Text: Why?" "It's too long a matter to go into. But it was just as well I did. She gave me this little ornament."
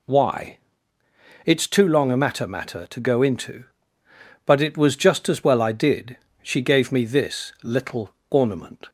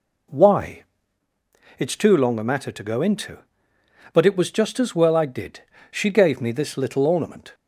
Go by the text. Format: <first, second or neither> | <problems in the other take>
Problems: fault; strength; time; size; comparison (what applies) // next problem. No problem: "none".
second | says "matter" twice; at 2.4 s // pauses between "little" and "ornament"; slight; at 8.1 s; 0.16 s long